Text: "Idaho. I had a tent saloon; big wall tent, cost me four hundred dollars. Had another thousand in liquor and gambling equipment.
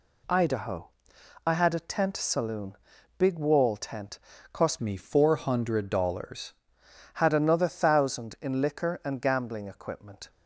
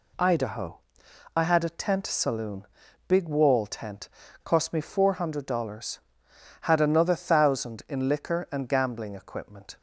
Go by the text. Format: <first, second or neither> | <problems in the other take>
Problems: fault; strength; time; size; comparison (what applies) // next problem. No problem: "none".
second | changes voice from "me" to "dollars"; from 4.8 to 6.5 s; 1.7 s long